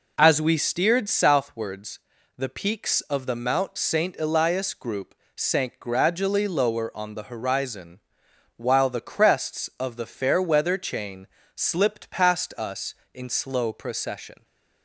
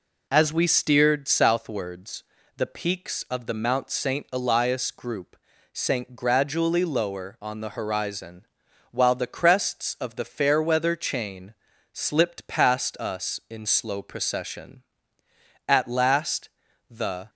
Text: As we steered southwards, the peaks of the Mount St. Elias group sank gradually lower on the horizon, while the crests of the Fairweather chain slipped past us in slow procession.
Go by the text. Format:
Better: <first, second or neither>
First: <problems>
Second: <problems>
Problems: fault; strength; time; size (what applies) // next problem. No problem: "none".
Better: first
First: pauses between "group" and "sank"; slight; at 5.1 s; 0.22 s long // pauses between "chain" and "slipped"; slight; at 11.2 s; 0.30 s long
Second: pauses between "group" and "sank"; slight; at 5.3 s; 0.34 s long // pauses between "chain" and "slipped"; at 11.5 s; 0.40 s long // goes on to say "At last the"; from 15.6 s on; 1.6 s long